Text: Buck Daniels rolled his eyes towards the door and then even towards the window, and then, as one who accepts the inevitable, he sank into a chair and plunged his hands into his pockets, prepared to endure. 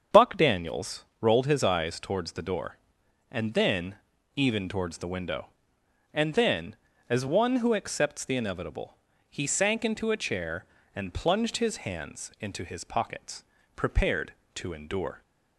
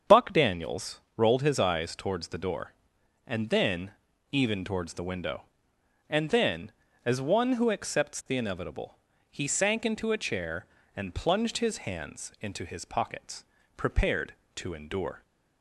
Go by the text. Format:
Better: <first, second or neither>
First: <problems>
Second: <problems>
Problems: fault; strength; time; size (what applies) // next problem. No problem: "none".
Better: neither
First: starts louder than the rest; strong; until 1.3 s; 7.5 dB // pauses between "Daniels" and "rolled"; slight; at 1.0 s; 0.16 s long // pauses between "then" and "even"; at 3.9 s; 0.40 s long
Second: starts louder than the rest; strong; until 1.2 s; 7 dB // pauses between "Daniels" and "rolled"; slight; at 0.9 s; 0.16 s long // pauses between "then" and "even"; at 3.9 s; 0.40 s long